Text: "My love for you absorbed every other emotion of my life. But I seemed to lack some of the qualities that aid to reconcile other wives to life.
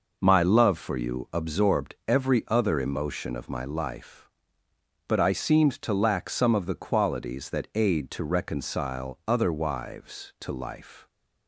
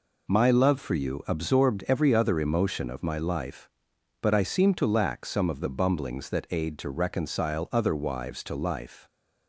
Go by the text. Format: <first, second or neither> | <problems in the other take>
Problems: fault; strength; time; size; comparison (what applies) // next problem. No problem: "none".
first | says "bumblings" for "qualities"; at 5.6 s